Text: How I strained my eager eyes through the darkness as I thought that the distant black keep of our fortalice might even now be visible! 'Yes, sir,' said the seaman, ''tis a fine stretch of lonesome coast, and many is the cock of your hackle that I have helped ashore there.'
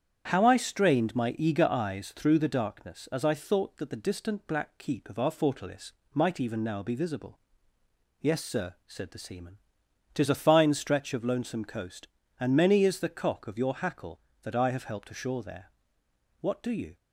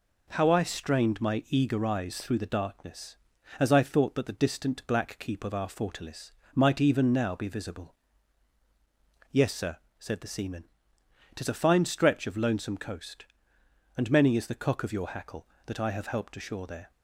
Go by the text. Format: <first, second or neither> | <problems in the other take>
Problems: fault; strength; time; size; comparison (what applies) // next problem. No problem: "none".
second | starts louder than the rest; strong; until 1.3 s; 8.5 dB // pauses between "fortalice" and "might"; slight; at 5.9 s; 0.22 s long; slight in the second // goes on to say "What do you"; from 16.4 s on; 0.56 s long